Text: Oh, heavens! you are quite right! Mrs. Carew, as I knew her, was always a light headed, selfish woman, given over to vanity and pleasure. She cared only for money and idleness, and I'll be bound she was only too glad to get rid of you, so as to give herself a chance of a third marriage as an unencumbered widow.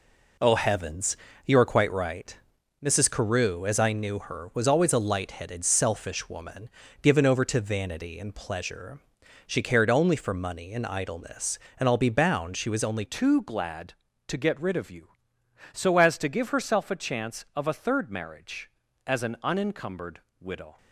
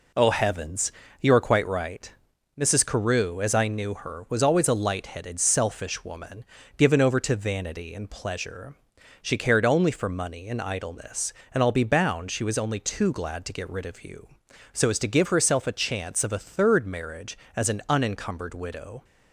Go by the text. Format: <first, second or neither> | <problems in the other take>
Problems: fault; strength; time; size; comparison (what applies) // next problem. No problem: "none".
second | changes voice at "too"; from 13.0 s on; 7.7 s long // pauses between "unencumbered" and "widow"; slight; at 20.2 s; 0.18 s long